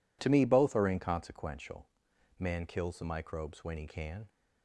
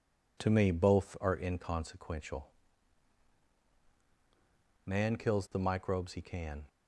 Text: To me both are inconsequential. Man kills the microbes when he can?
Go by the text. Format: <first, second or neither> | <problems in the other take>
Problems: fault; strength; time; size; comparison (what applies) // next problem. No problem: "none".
first | skips "when"; at 6.1 s